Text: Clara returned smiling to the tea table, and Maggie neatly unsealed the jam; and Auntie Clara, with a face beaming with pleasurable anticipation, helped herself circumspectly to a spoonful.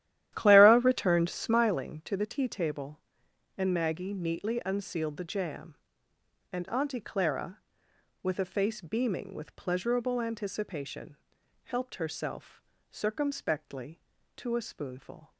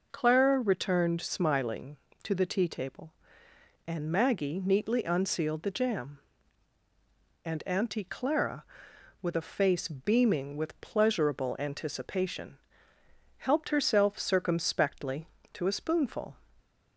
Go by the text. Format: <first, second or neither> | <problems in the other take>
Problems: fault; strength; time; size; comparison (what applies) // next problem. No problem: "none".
second | starts louder than the rest; strong; until 1.8 s; 12.5 dB // pauses between "herself" and "circumspectly"; slight; at 12.6 s; 0.28 s long